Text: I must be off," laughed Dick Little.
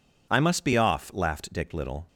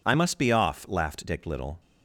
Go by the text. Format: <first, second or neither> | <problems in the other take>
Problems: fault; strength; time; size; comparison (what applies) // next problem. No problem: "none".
neither | none